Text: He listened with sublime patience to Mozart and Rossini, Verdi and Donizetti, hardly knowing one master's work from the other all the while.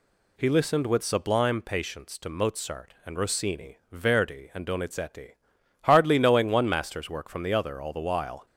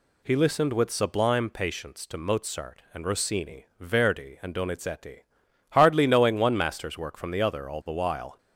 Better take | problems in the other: neither | none

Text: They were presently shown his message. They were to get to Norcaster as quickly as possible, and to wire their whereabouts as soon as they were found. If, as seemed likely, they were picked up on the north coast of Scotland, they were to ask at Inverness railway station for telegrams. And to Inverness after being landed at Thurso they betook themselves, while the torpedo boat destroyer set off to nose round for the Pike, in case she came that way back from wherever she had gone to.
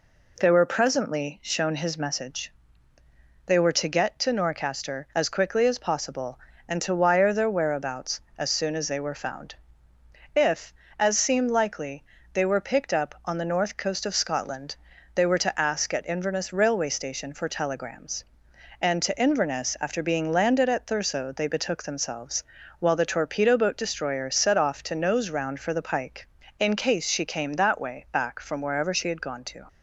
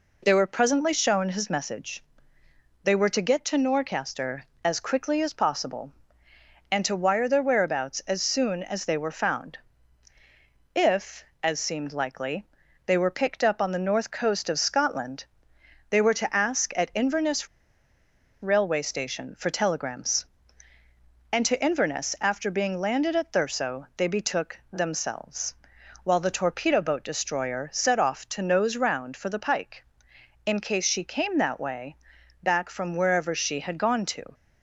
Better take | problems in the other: first | pauses between "Inverness" and "railway"; noticeable; at 17.4 s; 0.95 s long // pauses between "way" and "back"; noticeable; at 31.9 s; 0.48 s long

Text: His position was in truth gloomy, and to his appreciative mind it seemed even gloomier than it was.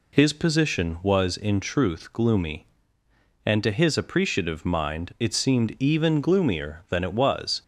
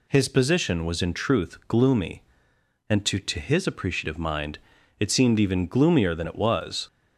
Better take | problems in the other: first | says "to" twice; at 3.1 s // pauses between "mind" and "it"; at 4.5 s; 0.42 s long

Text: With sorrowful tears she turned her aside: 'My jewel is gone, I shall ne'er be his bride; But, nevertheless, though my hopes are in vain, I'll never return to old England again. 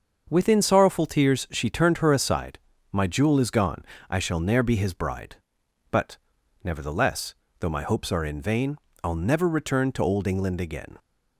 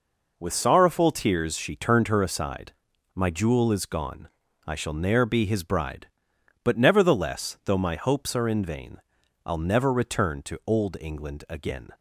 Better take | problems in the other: second | starts louder than the rest; until 1.3 s; 6.5 dB // says "Within" for "With"; at 0.3 s

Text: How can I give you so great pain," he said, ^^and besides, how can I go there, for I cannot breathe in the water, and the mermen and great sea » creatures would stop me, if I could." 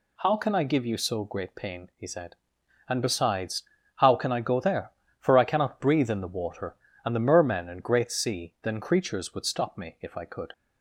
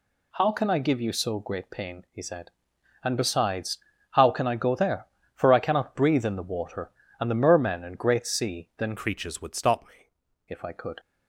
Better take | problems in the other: first | changes voice from "creatures" to "me"; from 8.9 to 10.0 s; 1.1 s long

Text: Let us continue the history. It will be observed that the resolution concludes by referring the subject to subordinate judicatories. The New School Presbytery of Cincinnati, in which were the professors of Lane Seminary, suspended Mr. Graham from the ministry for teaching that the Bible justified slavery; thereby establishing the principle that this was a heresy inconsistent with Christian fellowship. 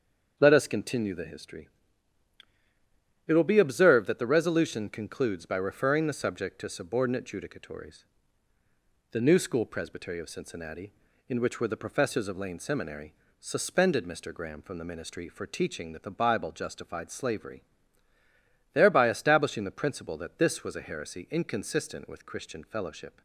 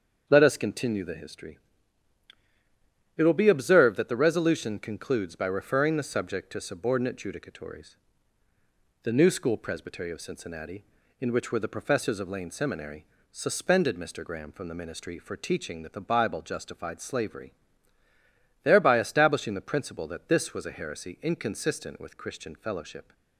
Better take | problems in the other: neither | starts louder than the rest; the same in both

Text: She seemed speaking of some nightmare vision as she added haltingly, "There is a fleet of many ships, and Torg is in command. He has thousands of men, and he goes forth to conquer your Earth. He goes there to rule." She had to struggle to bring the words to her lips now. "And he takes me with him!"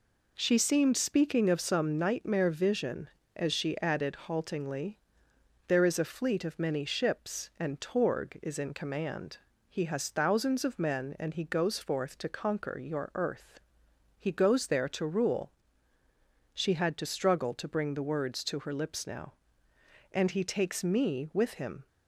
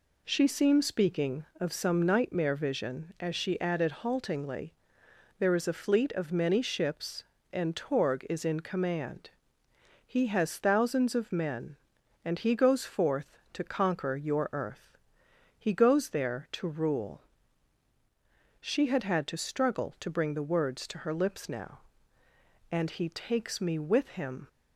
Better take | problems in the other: first | says "had" twice; at 19.0 s

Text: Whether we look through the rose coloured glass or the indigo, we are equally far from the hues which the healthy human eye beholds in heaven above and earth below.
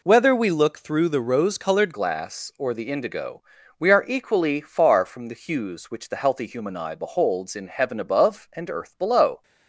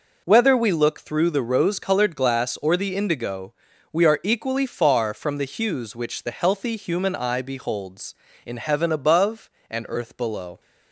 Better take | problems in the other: second | changes voice at "glass"; from 1.9 s on; 7.5 s long

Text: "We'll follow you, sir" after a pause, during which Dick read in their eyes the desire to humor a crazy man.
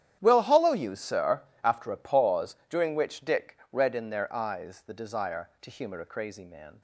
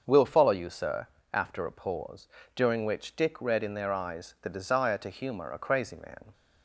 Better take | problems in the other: second | starts louder than the rest; strong; until 1.2 s; 10.5 dB; also in the second // says "hollow" for "follow"; at 0.4 s // pauses between "sir" and "after"; slight; at 1.4 s; 0.20 s long; slight in the second

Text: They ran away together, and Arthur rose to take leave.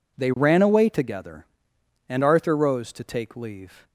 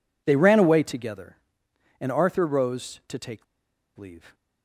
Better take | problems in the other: first | pauses between "take" and "leave"; noticeable; at 3.4 s; 0.53 s long

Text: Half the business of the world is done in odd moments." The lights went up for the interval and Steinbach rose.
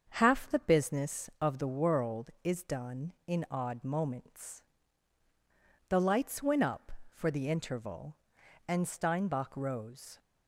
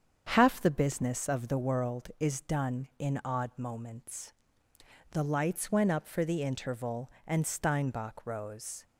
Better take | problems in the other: neither | starts louder than the rest; the same in both

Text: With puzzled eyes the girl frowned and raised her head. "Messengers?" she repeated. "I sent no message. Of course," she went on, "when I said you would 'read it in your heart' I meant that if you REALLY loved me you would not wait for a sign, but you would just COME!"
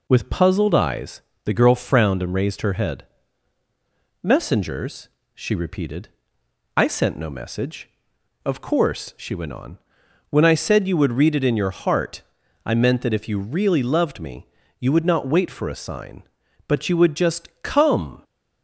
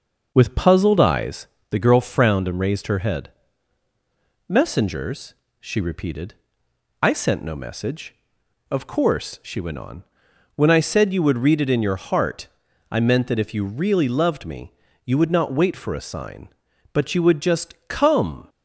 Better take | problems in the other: first | starts louder than the rest; noticeable; until 1.7 s; 6 dB // pauses between "eyes" and "the"; slight; at 1.4 s; 0.22 s long; slight in the first // pauses between "heart" and "I"; at 12.4 s; 0.44 s long; also in the first // pauses between "me" and "you"; slight; at 14.7 s; 0.32 s long; slight in the first

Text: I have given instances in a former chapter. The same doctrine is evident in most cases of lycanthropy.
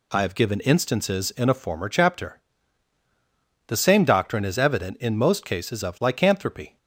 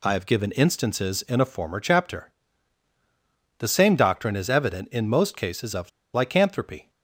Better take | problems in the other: first | pauses between "of" and "lycanthropy"; slight; at 5.8 s; 0.24 s long

